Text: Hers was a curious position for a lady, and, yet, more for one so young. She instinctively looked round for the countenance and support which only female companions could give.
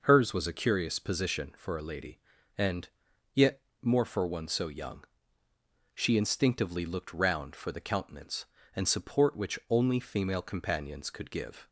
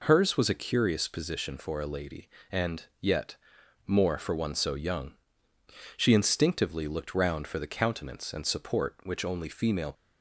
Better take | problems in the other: first | stops before "companions could give"; at 9.9 s

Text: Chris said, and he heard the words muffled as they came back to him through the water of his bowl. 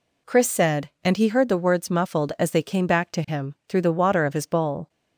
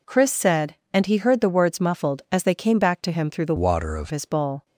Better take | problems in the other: first | changes voice from "water" to "of"; from 3.5 to 4.1 s; 0.6 s long

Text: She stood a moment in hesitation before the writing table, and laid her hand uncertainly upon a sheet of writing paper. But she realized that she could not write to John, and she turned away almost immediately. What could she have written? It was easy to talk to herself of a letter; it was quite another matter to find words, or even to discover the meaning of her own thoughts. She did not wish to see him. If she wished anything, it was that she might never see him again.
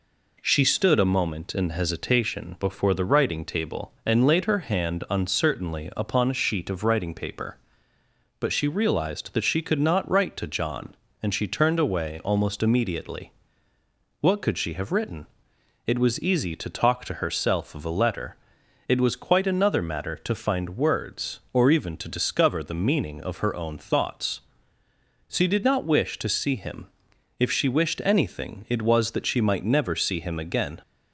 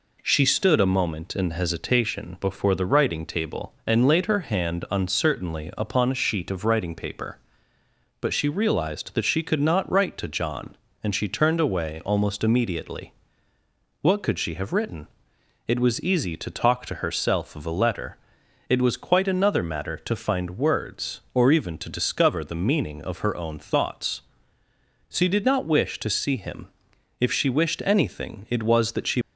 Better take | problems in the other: first | stops before "might never see him again"; at 29.2 s

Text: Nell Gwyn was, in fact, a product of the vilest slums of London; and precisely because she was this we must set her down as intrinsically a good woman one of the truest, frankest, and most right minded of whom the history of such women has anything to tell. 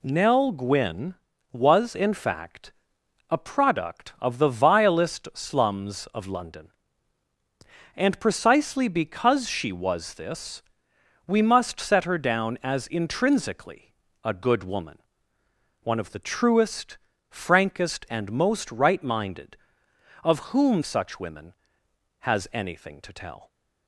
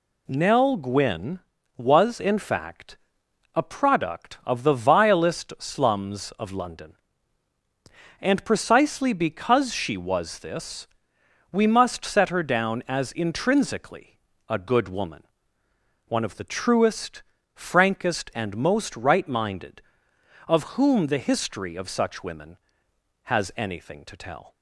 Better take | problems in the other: second | pauses between "this" and "we"; noticeable; at 10.6 s; 0.64 s long; noticeable in the second // pauses between "intrinsically" and "a"; slight; at 13.9 s; 0.32 s long; slight in the second // pauses between "woman" and "one"; noticeable; at 15.0 s; 0.80 s long; noticeable in the second // skips "the history of"; at 20.8 s

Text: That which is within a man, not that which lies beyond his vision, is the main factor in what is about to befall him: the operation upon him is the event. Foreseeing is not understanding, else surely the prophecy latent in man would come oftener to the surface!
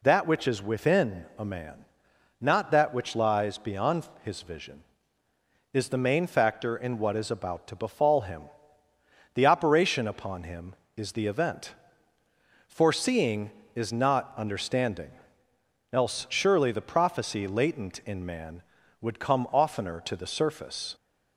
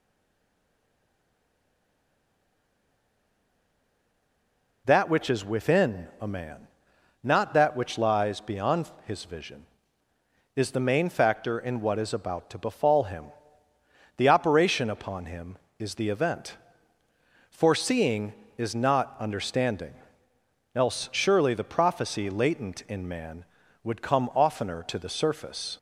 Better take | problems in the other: first | stays silent before the first word; strong; until 4.8 s; 4.8 s long // pauses between "beyond" and "his"; slight; at 8.8 s; 0.16 s long; slight in the first

